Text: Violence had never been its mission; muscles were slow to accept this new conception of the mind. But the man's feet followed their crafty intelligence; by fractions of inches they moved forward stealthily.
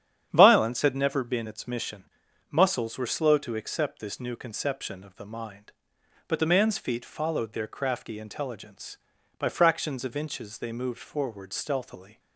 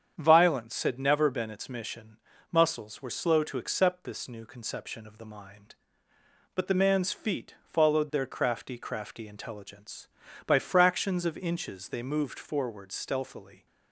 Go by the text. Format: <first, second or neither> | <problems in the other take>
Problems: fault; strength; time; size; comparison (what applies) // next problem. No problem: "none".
first | starts louder than the rest; strong; until 1.1 s; 8 dB; strong in the first // says "crafty" twice; at 8.7 s